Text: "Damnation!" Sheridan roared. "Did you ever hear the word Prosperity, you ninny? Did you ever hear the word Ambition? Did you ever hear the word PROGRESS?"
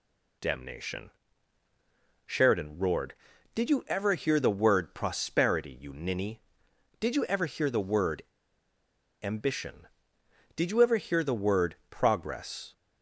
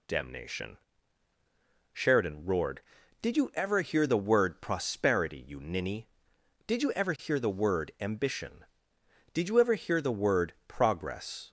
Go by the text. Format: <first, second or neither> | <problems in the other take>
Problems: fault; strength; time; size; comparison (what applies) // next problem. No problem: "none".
second | pauses between "word" and "Ambition"; at 8.2 s; 1.0 s long // pauses between "word" and "PROGRESS"; slight; at 11.7 s; 0.16 s long; slight in the second